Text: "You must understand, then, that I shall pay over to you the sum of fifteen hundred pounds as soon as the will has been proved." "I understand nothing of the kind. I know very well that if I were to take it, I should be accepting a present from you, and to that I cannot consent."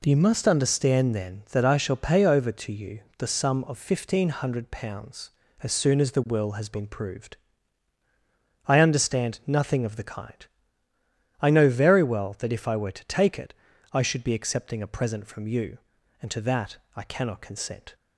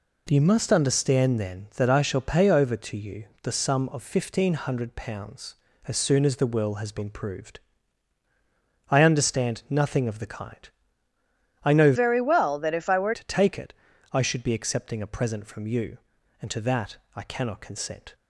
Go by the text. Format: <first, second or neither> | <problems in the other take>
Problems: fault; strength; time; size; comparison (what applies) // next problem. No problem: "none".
first | pauses between "you" and "the"; slight; at 3.2 s; 0.16 s long; slight in the first // changes voice from "very" to "were"; from 11.9 to 13.1 s; 1.2 s long // pauses between "that" and "I"; slight; at 16.9 s; 0.18 s long; slight in the first